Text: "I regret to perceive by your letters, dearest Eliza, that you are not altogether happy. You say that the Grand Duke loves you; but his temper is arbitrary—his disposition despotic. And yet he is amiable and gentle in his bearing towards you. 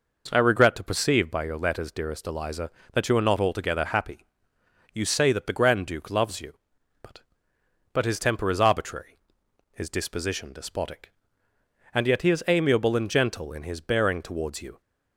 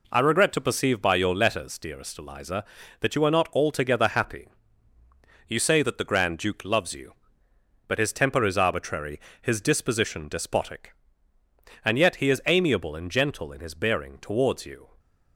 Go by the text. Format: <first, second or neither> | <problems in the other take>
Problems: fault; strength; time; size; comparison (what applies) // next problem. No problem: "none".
second | says "but" twice; at 7.9 s